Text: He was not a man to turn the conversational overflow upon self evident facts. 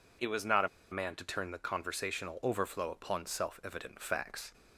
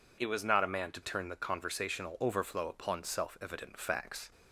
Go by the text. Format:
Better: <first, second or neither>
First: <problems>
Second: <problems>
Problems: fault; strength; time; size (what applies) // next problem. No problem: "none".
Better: second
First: pauses between "a" and "man"; slight; at 0.6 s; 0.23 s long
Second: none